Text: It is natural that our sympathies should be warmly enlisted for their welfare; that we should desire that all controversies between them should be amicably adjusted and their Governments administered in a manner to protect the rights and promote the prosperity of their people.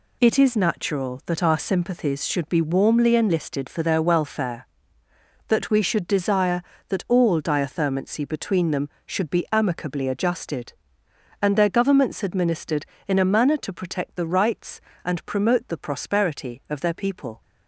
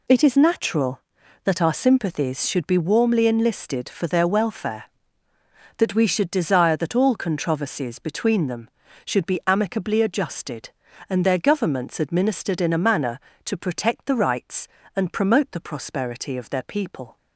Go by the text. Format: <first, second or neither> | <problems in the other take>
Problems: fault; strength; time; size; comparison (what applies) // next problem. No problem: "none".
second | says "diathermancy" for "controversies"; at 7.4 s